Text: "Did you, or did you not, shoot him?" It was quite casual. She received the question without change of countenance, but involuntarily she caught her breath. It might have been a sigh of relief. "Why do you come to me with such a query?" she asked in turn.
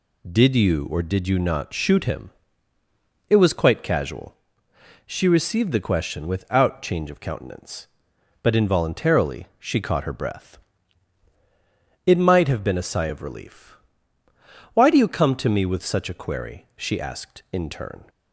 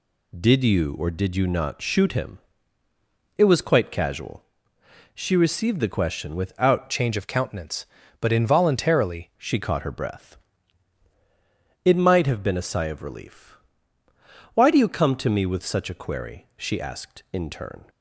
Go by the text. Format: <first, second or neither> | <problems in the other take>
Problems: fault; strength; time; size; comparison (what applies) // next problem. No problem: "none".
first | changes voice from "change" to "involuntarily"; from 6.9 to 9.3 s; 2.4 s long